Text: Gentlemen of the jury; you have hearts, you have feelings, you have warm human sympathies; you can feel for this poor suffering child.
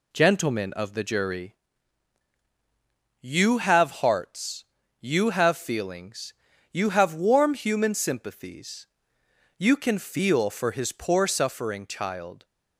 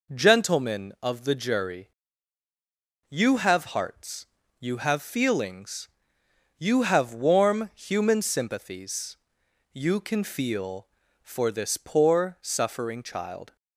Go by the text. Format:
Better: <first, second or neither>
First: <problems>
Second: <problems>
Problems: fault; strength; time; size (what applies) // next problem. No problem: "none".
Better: second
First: says "his" for "this"; at 10.7 s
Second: none